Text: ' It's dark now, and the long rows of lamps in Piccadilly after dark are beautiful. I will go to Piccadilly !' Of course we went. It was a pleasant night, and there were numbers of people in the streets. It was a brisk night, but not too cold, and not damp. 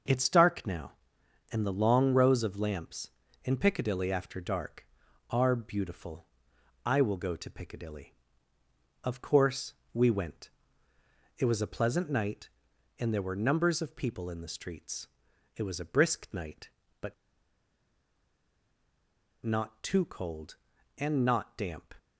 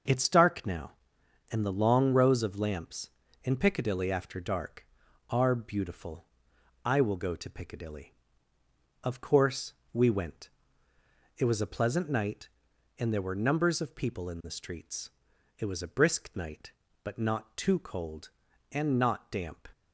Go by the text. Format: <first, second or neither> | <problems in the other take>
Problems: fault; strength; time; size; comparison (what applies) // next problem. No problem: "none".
second | starts louder than the rest; until 1.6 s; 6.5 dB; also in the second // pauses between "course" and "we"; slight; at 9.7 s; 0.20 s long; slight in the second // pauses between "but" and "not"; strong; at 17.1 s; 2.3 s long